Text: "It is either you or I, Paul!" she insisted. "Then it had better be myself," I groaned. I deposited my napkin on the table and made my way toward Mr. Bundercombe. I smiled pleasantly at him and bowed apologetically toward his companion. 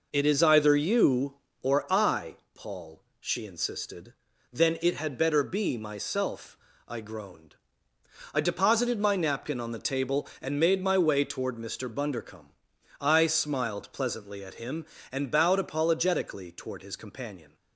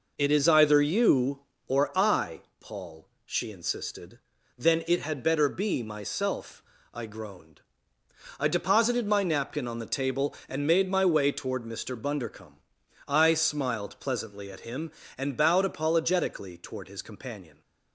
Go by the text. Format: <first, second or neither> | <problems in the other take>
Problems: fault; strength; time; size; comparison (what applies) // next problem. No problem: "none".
neither | none